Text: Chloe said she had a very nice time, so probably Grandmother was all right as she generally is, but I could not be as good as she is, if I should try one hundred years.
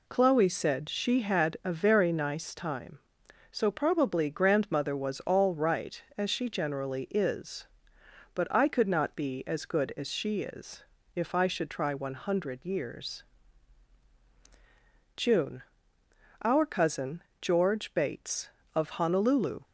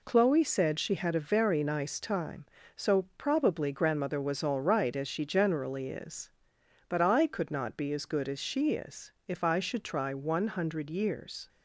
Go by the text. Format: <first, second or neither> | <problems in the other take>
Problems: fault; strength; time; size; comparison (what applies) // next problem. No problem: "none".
second | goes on to say "June Our cousin George Bates of Honolulu"; strong; from 15.1 s on; 4.4 s long